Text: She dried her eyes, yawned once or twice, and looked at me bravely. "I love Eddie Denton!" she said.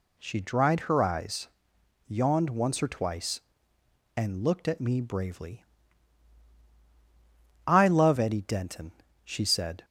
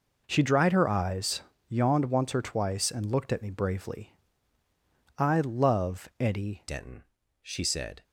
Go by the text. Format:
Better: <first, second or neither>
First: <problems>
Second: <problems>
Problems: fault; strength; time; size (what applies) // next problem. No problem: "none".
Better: first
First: none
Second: changes voice at "Denton"; from 6.6 s on; 1.4 s long